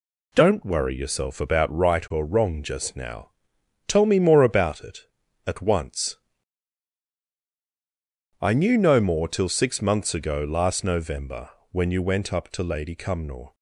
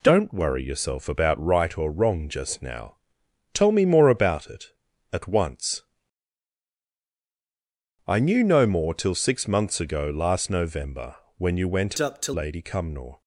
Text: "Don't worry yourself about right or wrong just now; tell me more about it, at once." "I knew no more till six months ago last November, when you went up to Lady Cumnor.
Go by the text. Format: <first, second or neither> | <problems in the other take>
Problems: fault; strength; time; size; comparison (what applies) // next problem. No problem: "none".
first | changes voice from "up" to "to"; from 11.9 to 12.3 s; 0.4 s long